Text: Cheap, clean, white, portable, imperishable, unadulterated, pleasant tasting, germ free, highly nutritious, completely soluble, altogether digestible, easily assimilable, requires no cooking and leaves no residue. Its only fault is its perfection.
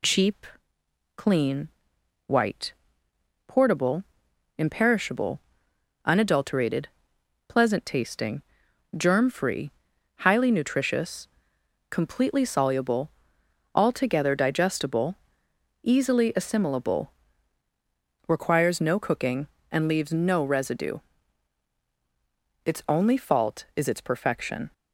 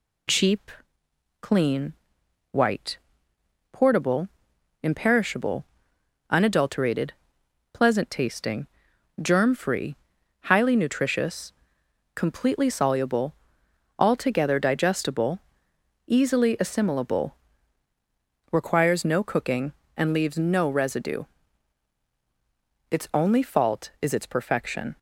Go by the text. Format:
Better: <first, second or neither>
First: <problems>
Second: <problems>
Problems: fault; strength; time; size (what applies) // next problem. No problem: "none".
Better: neither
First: none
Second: none